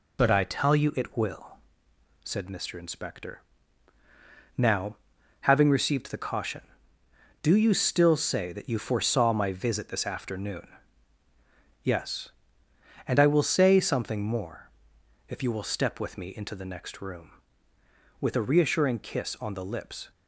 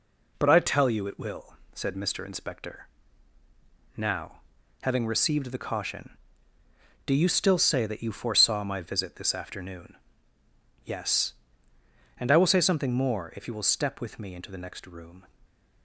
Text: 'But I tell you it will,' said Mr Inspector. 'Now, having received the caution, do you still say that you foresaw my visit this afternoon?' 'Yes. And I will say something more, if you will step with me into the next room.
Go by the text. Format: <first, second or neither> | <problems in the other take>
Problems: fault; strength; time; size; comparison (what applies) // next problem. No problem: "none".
second | goes on to say "With a reassuring kiss on the lips"; strong; from 18.2 s on; 1.9 s long